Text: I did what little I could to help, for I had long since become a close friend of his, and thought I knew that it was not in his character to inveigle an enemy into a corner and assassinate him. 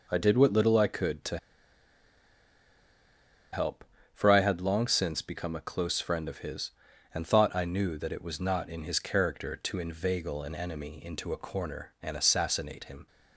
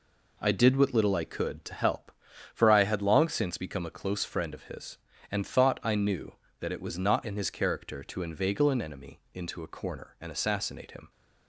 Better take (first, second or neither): second